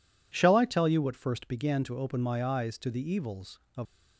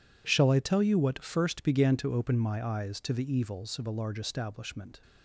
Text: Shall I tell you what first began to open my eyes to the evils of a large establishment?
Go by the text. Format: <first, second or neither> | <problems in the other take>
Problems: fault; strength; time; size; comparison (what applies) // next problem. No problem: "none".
second | stops before "a large establishment"; at 3.8 s